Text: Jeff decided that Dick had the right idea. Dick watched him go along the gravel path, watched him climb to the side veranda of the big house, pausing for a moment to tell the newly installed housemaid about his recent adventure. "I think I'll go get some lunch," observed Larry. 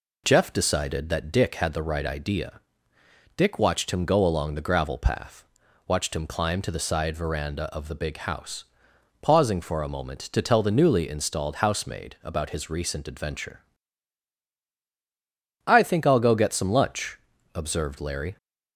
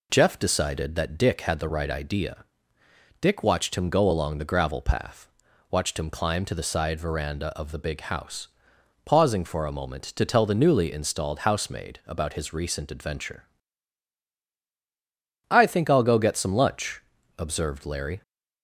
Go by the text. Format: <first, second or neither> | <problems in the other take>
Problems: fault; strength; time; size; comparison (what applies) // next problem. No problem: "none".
neither | none